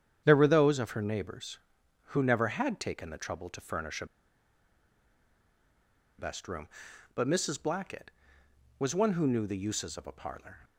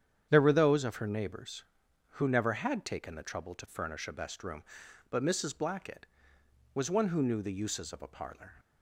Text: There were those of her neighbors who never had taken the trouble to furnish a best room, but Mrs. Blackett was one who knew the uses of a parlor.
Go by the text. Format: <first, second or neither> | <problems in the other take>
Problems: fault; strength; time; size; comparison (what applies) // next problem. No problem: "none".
second | starts louder than the rest; strong; until 1.2 s; 8.5 dB; strong in the second // pauses between "a" and "best"; strong; at 4.0 s; 2.1 s long